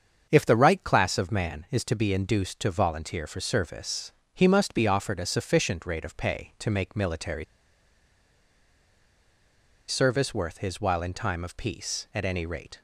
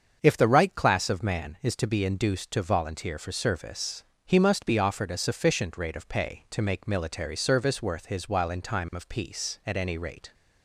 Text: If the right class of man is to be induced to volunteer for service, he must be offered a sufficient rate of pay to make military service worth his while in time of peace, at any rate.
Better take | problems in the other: second | starts louder than the rest; until 1.3 s; 7 dB; also in the second // pauses between "military" and "service"; strong; at 7.4 s; 2.4 s long

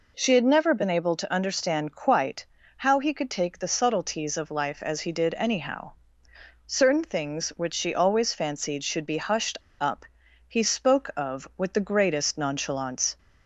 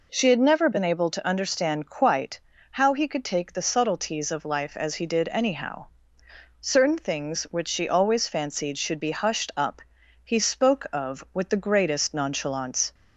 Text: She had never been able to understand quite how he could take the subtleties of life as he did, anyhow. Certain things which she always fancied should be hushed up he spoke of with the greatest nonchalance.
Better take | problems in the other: second | pauses between "quite" and "how"; slight; at 2.4 s; 0.30 s long; slight in the second // pauses between "hushed" and "up"; slight; at 9.5 s; 0.20 s long // pauses between "up" and "he"; at 10.0 s; 0.42 s long; also in the second

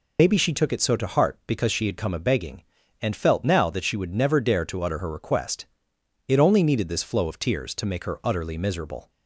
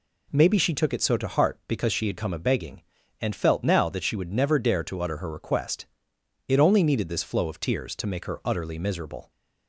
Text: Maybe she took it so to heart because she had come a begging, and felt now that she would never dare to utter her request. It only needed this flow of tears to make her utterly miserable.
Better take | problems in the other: second | loses the start of "Maybe"; at 0.1 s; 115 ms

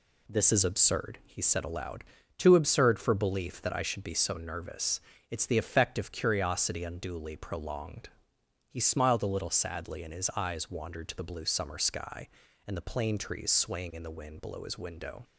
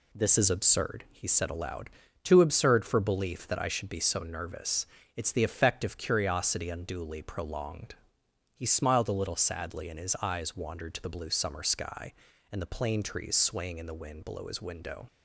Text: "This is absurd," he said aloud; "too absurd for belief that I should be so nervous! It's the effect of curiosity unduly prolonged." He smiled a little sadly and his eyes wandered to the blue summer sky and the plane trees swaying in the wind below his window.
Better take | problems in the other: neither | none

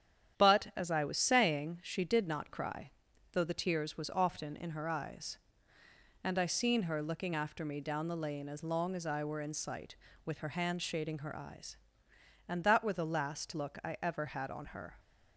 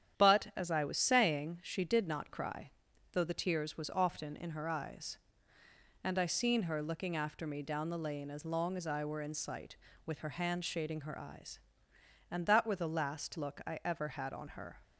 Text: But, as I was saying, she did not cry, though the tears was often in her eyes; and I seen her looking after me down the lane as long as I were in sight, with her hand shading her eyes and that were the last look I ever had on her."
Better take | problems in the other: neither | starts louder than the rest; strong; the same in both

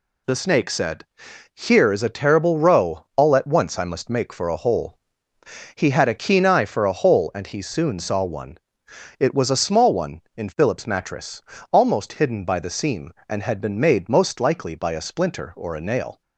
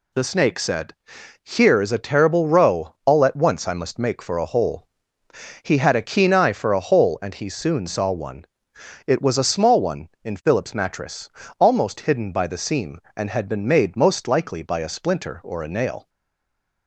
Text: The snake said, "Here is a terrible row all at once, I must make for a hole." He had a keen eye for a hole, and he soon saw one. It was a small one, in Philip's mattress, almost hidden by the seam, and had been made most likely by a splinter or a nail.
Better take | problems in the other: first | stays silent after the last word; slight; from 16.0 s on; 0.8 s long

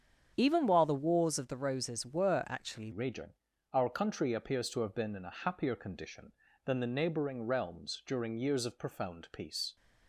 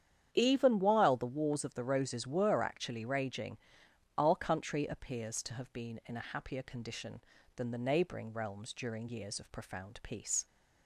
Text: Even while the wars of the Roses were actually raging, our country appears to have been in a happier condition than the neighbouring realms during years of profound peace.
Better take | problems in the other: second | starts louder than the rest; strong; until 1.3 s; 8 dB; strong in the second // changes voice at "raging"; from 2.9 s on; 6.8 s long

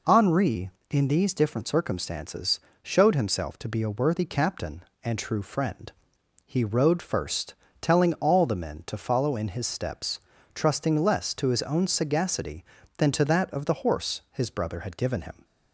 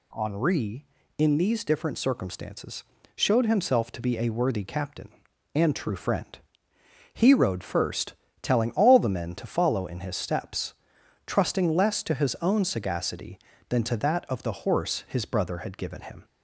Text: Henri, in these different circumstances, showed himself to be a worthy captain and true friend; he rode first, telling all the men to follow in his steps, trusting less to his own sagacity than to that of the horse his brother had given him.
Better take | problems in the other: neither | none

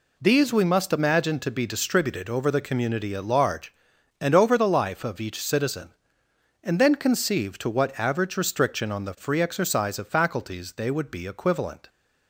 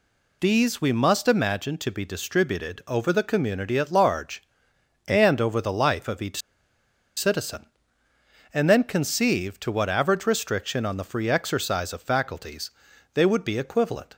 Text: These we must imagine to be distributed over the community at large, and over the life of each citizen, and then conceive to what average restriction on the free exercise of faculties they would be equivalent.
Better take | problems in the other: first | pauses between "each" and "citizen"; noticeable; at 6.4 s; 0.76 s long // pauses between "faculties" and "they"; at 12.7 s; 0.42 s long

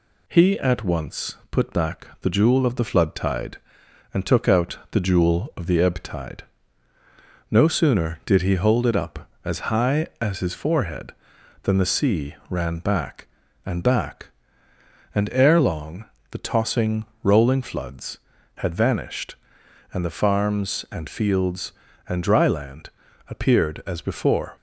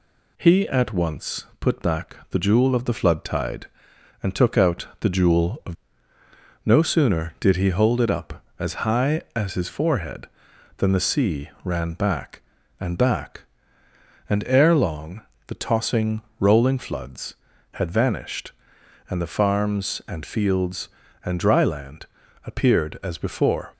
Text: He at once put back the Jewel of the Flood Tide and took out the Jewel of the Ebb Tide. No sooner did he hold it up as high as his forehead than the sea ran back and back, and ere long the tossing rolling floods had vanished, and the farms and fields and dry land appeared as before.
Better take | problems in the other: first | skips "the Ebb Tide"; at 6.1 s // pauses between "sea" and "ran"; slight; at 11.4 s; 0.16 s long; slight in the first // pauses between "long" and "the"; slight; at 15.2 s; 0.24 s long; slight in the first // pauses between "tossing" and "rolling"; slight; at 16.2 s; 0.18 s long; slight in the first // pauses between "land" and "appeared"; at 22.0 s; 0.40 s long; also in the first

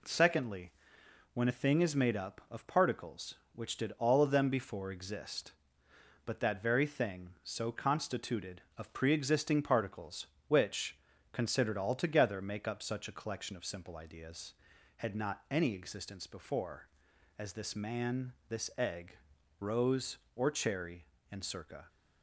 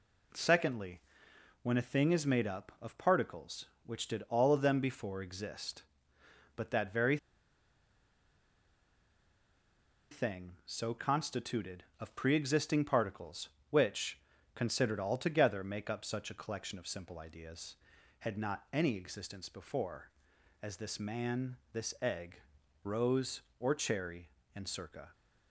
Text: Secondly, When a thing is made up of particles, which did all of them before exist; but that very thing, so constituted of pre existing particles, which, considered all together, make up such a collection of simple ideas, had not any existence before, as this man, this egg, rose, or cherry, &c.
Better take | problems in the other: first | pauses between "very" and "thing"; strong; at 7.1 s; 2.9 s long

